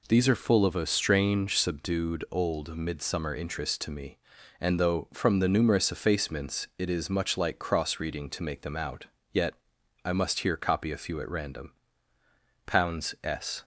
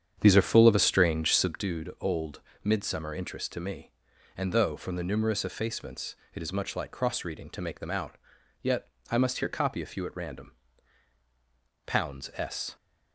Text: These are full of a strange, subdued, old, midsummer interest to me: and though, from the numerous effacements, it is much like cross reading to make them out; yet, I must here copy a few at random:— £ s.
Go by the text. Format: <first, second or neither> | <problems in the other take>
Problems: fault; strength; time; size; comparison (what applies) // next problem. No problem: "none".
first | starts louder than the rest; strong; until 1.6 s; 8.5 dB